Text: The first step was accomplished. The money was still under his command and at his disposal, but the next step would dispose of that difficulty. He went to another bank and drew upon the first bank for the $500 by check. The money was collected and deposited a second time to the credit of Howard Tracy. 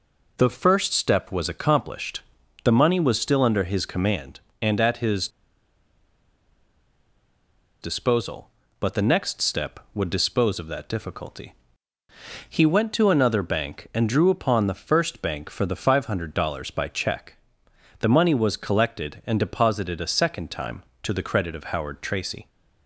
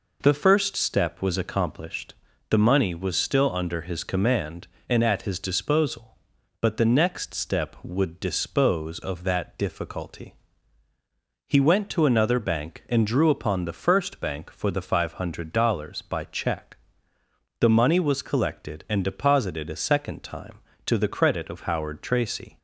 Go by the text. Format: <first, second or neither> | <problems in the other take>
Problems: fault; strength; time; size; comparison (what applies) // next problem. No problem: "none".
second | pauses between "his" and "disposal"; strong; at 5.2 s; 2.5 s long